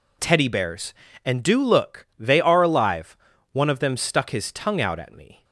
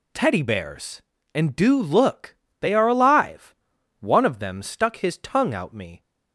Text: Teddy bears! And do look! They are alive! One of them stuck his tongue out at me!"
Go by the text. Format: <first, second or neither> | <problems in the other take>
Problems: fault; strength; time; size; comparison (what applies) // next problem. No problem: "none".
first | skips "at"; at 5.7 s